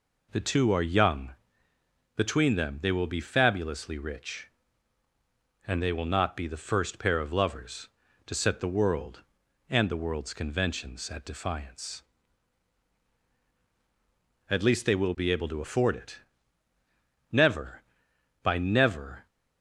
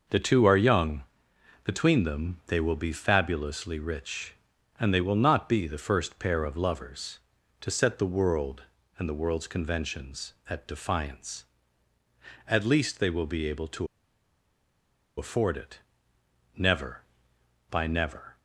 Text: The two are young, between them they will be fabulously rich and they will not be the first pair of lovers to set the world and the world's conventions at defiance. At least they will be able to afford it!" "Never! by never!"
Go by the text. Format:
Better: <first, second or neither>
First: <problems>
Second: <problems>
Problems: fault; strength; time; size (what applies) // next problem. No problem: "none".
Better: first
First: none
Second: pauses between "to" and "afford"; strong; at 13.8 s; 1.3 s long